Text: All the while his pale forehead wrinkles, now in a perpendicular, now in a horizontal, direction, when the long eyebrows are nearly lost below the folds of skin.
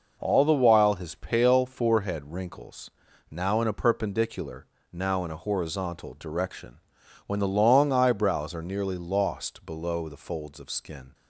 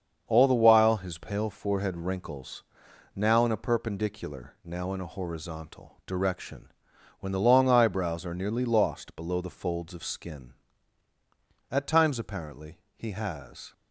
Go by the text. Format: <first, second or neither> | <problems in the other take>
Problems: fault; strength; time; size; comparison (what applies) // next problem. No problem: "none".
first | starts louder than the rest; until 1.2 s; 7 dB // goes on to say "At times apparently he has"; strong; from 11.7 s on; 2.0 s long